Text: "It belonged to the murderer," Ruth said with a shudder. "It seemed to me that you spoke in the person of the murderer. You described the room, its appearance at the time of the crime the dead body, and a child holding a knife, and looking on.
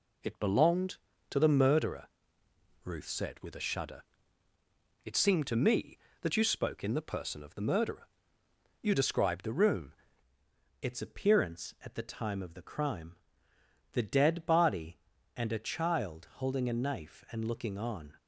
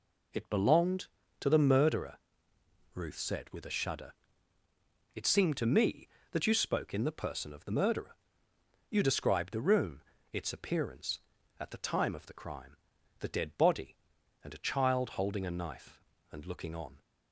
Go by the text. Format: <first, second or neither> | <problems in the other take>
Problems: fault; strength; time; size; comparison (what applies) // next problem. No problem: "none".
second | changes voice at "its"; from 10.8 s on; 7.3 s long // pauses between "crime" and "the"; noticeable; at 13.1 s; 0.76 s long; also in the second